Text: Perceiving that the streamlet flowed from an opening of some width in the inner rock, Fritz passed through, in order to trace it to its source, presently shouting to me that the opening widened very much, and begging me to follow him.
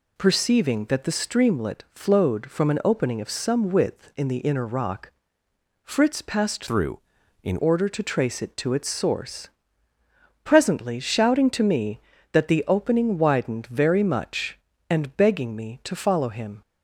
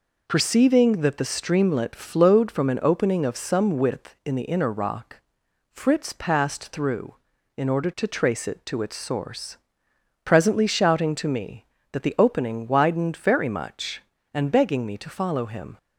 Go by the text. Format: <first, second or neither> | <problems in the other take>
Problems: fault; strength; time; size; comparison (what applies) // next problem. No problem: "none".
second | changes voice from "through" to "in"; from 6.6 to 7.5 s; 0.9 s long